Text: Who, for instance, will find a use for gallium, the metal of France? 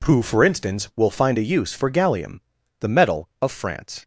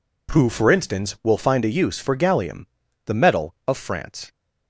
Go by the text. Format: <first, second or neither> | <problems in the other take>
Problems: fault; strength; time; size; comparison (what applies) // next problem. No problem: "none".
neither | none